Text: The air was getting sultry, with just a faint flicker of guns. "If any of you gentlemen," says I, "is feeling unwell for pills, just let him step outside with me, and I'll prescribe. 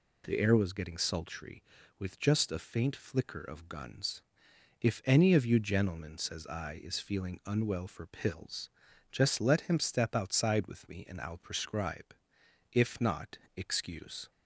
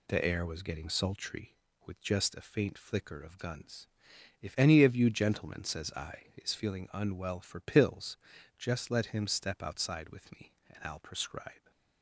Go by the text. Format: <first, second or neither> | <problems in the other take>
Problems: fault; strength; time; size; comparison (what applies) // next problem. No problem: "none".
second | goes on to say "If not excuse"; from 12.7 s on; 1.5 s long